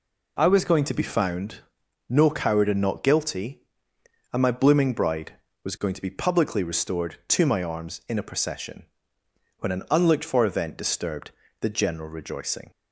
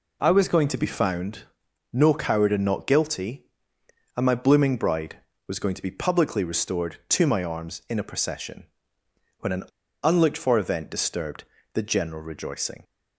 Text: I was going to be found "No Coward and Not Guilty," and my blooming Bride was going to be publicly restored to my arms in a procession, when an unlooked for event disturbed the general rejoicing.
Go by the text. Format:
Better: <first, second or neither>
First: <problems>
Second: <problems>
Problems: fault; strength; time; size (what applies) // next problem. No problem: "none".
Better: first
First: pauses between "found" and "No"; noticeable; at 1.6 s; 0.46 s long // pauses between "disturbed" and "the"; slight; at 11.3 s; 0.30 s long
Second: pauses between "found" and "No"; noticeable; at 1.4 s; 0.46 s long // pauses between "an" and "unlooked"; at 9.6 s; 0.40 s long // pauses between "disturbed" and "the"; slight; at 11.4 s; 0.30 s long